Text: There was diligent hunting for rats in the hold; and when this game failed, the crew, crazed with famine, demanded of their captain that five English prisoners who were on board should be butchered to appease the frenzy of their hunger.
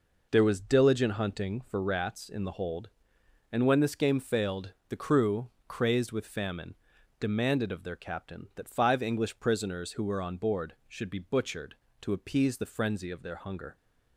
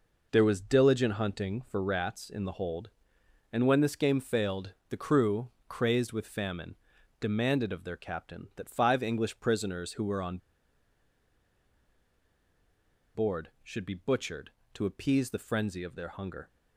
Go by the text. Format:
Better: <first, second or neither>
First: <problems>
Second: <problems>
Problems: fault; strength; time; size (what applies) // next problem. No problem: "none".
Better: first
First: none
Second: pauses between "on" and "board"; strong; at 10.3 s; 2.7 s long